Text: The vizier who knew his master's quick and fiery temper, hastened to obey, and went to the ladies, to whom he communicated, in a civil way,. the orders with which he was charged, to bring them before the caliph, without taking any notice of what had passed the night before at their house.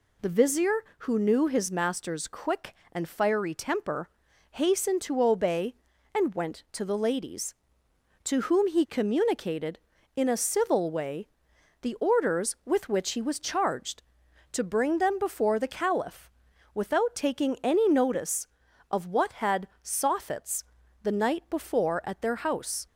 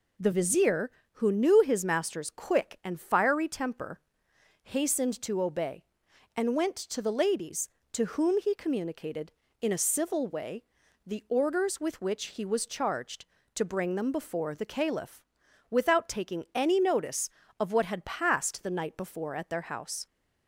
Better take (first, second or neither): second